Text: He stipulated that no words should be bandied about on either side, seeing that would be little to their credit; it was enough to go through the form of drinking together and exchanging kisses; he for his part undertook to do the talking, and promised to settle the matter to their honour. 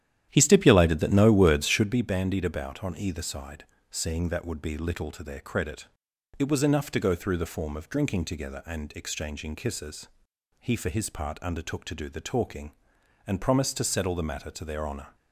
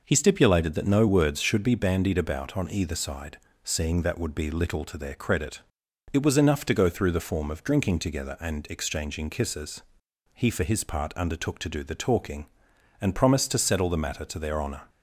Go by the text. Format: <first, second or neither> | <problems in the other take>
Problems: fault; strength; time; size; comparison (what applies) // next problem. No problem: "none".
second | starts louder than the rest; strong; until 2.0 s; 11 dB